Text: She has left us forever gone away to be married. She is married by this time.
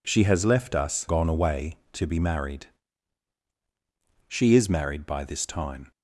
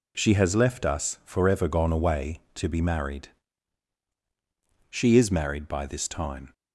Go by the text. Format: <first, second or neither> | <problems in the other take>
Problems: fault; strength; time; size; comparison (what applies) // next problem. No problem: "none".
second | skips "forever"; at 1.0 s